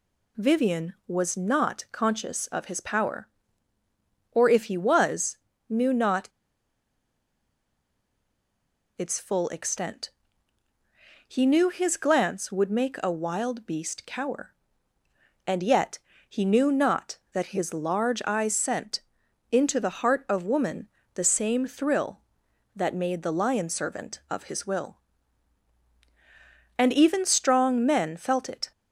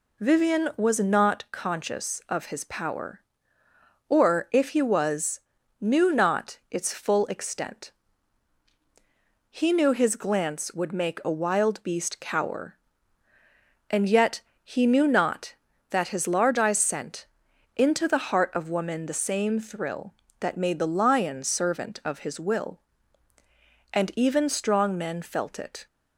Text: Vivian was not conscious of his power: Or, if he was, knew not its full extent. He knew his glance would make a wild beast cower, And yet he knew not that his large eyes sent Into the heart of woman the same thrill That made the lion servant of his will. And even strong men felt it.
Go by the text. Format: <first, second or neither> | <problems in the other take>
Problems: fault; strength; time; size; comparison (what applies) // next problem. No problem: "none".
second | pauses between "not" and "its"; strong; at 6.2 s; 2.7 s long // pauses between "yet" and "he"; slight; at 15.9 s; 0.28 s long; slight in the second // pauses between "sent" and "Into"; noticeable; at 19.0 s; 0.48 s long; noticeable in the second // pauses between "woman" and "the"; slight; at 20.8 s; 0.24 s long